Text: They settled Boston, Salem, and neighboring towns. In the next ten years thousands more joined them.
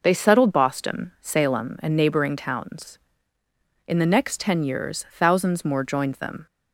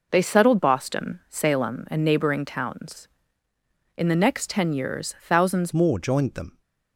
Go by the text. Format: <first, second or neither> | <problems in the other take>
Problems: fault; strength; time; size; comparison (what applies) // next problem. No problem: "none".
first | changes voice at "more"; from 5.7 s on; 0.9 s long